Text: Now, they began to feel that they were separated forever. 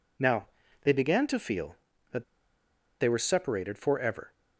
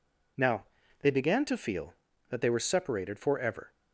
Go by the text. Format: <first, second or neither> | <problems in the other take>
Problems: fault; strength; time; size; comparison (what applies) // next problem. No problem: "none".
second | pauses between "that" and "they"; noticeable; at 2.2 s; 0.77 s long